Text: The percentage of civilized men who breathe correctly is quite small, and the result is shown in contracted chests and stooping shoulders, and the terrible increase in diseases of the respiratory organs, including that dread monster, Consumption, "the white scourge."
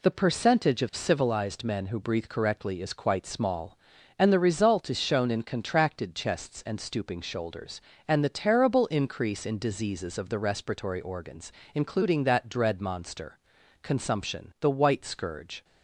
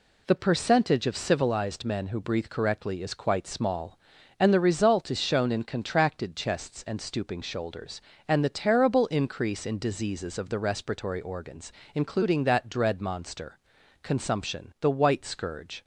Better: neither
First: none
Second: none

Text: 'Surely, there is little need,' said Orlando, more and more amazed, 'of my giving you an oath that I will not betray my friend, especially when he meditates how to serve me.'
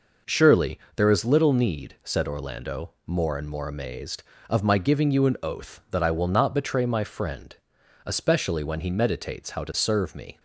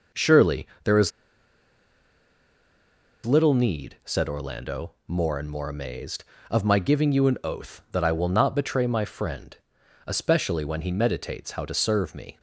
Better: first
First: none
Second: pauses between "is" and "little"; strong; at 1.1 s; 2.1 s long

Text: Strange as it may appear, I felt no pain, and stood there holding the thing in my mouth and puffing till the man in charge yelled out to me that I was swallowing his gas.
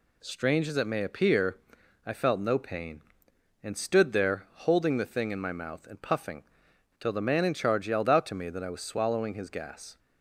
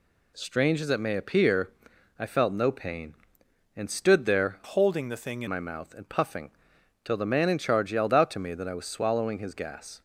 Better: first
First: pauses between "puffing" and "till"; noticeable; at 6.4 s; 0.54 s long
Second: changes voice from "holding" to "in"; from 4.6 to 5.4 s; 0.8 s long // pauses between "puffing" and "till"; noticeable; at 6.5 s; 0.52 s long

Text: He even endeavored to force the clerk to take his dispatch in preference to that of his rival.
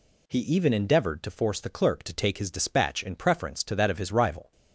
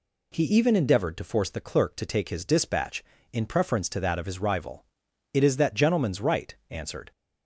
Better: first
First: none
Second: goes on to say "It is that gentleman's right answered"; strong; from 5.3 s on; 1.7 s long

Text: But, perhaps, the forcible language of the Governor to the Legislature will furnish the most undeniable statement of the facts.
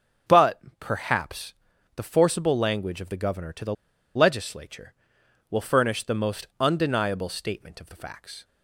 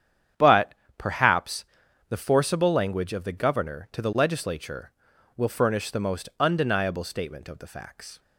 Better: second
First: starts louder than the rest; strong; until 1.4 s; 7.5 dB // pauses between "the" and "Legislature"; at 3.7 s; 0.41 s long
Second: starts louder than the rest; strong; until 1.5 s; 9 dB

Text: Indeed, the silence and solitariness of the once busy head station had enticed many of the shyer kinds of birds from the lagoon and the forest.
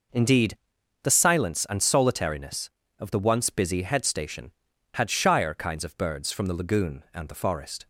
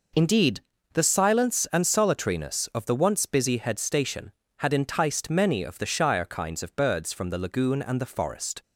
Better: second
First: skips "enticed many of the"; at 5.0 s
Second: none

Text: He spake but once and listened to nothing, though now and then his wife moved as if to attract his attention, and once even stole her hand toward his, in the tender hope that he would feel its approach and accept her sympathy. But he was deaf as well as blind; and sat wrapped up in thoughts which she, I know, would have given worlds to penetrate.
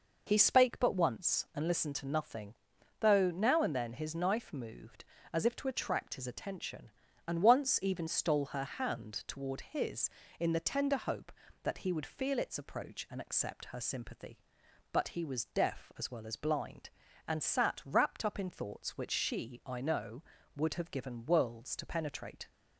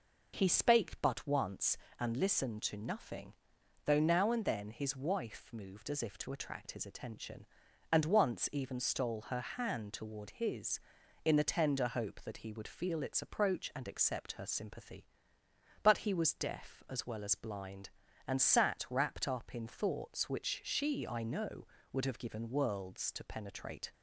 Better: second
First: says "knife" for "wife"; at 4.1 s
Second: none

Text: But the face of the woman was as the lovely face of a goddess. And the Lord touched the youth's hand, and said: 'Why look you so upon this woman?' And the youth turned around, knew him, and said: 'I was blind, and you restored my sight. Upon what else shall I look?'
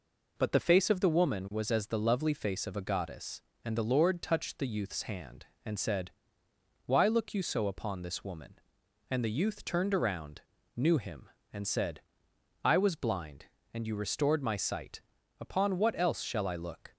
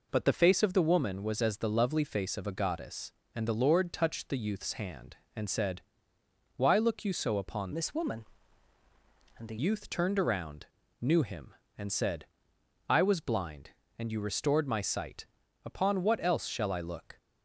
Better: first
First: none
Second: changes voice from "this" to "the"; from 7.7 to 9.5 s; 1.8 s long

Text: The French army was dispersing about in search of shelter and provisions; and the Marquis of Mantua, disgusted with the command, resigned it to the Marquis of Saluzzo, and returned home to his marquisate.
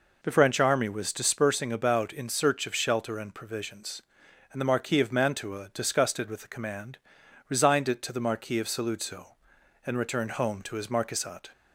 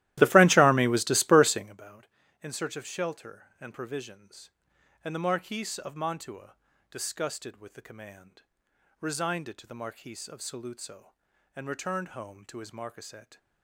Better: first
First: none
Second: starts louder than the rest; strong; until 1.8 s; 15.5 dB

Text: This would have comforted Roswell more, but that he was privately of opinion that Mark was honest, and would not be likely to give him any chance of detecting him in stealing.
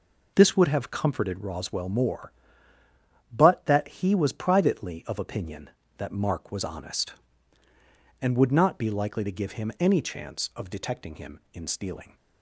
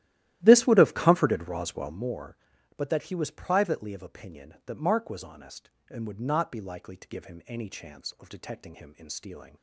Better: first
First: none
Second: starts louder than the rest; strong; until 2.1 s; 14 dB

